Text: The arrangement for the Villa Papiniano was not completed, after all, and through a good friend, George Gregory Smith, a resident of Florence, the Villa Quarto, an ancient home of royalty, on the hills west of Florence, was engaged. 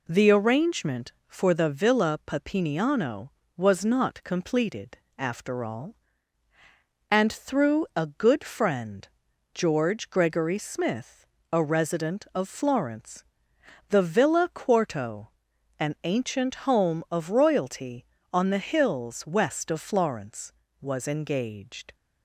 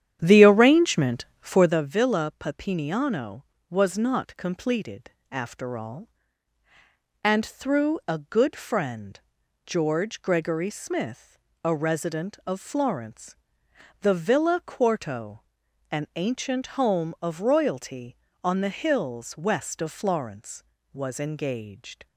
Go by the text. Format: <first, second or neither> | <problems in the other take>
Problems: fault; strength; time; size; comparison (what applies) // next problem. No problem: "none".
first | starts louder than the rest; strong; until 1.8 s; 10 dB